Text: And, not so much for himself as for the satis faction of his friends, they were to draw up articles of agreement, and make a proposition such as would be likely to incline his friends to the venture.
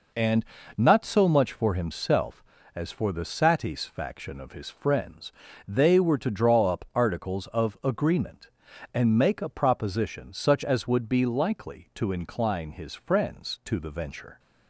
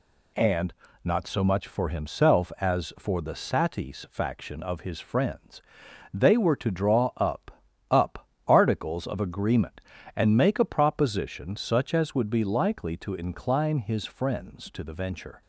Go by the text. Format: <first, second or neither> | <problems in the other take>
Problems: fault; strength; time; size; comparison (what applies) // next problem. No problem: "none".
first | says "up" twice; at 7.9 s